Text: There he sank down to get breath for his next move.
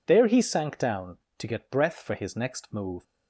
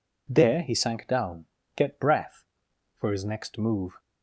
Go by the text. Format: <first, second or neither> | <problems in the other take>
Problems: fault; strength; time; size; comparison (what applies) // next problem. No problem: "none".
first | skips "to"; at 1.6 s